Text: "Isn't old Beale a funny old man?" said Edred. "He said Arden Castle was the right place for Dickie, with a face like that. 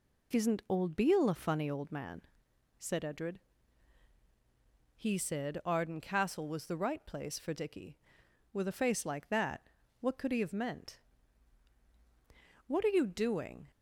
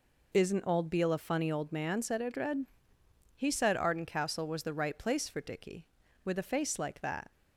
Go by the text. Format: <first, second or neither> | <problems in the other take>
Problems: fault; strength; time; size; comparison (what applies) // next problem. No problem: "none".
second | goes on to say "What could he have meant What are you doing"; strong; from 10.0 s on; 3.7 s long